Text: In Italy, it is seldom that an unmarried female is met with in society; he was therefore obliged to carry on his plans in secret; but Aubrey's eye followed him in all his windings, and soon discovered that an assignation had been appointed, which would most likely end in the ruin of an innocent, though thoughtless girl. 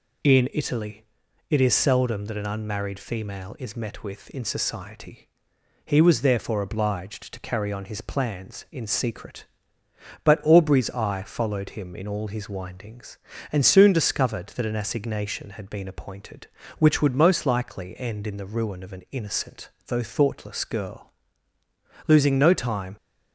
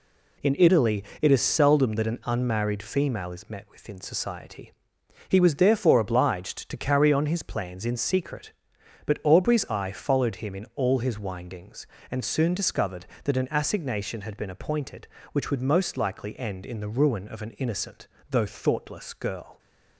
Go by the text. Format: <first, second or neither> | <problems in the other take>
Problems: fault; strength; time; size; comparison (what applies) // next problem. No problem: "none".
second | goes on to say "Losing no time"; noticeable; from 22.0 s on; 0.90 s long